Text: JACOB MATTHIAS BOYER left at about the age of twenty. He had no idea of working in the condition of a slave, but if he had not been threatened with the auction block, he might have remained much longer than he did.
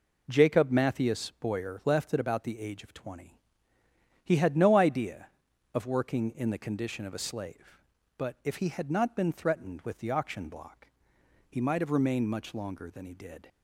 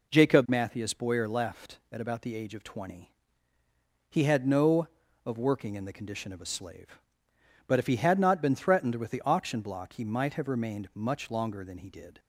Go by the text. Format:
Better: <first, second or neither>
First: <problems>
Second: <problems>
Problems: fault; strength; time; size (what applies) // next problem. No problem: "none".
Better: first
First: none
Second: skips "idea"; at 5.0 s